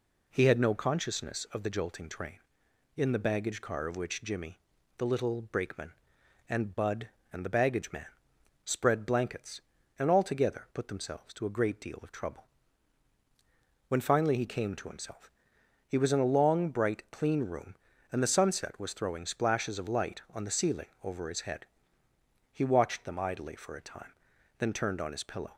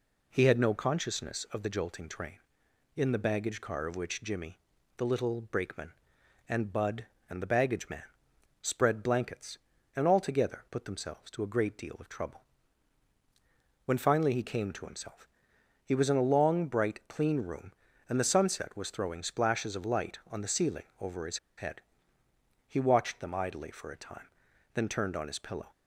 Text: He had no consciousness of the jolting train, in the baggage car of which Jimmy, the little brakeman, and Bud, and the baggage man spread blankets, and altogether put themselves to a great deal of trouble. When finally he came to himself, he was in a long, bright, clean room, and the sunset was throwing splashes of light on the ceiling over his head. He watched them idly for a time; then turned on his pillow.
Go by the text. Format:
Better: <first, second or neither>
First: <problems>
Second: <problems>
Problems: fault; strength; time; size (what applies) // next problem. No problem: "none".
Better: first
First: pauses between "man" and "spread"; noticeable; at 8.0 s; 0.56 s long // pauses between "ceiling" and "over"; slight; at 20.8 s; 0.16 s long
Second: pauses between "man" and "spread"; noticeable; at 8.0 s; 0.56 s long // pauses between "ceiling" and "over"; slight; at 20.8 s; 0.16 s long // pauses between "his" and "head"; slight; at 21.3 s; 0.20 s long